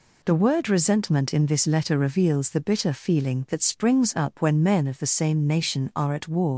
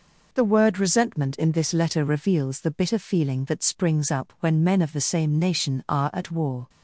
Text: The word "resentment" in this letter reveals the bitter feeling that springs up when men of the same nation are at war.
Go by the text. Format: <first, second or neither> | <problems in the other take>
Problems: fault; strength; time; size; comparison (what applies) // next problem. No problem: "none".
second | leaves "war" unfinished; at 6.5 s; 105 ms